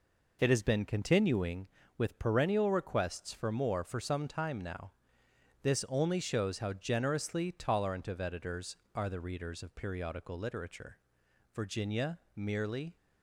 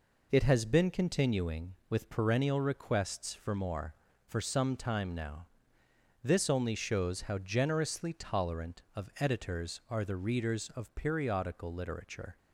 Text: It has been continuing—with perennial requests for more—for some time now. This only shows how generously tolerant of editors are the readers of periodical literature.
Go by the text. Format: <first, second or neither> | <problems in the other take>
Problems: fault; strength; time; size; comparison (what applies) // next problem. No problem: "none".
second | goes on to say "Virginia merely"; from 11.5 s on; 1.4 s long